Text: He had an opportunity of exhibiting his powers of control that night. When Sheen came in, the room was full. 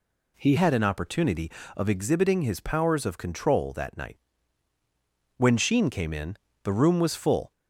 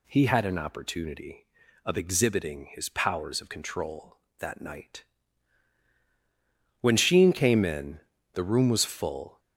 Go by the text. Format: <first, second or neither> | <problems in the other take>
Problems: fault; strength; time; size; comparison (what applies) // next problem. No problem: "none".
second | changes voice at "had"; from 0.5 s on; 7.0 s long